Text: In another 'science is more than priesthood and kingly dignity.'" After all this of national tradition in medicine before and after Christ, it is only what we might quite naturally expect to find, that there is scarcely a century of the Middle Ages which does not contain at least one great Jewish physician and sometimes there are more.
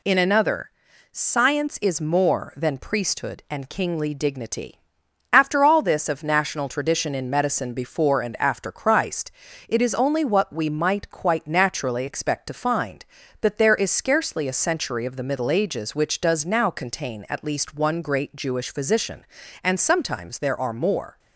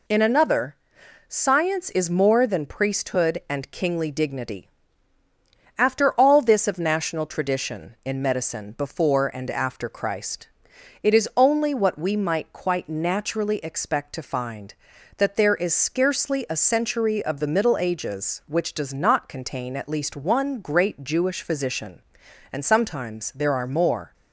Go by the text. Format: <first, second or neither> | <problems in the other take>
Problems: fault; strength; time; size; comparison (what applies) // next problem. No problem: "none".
second | pauses between "another" and "science"; at 0.7 s; 0.42 s long; noticeable in the second // says "now" for "not"; at 16.4 s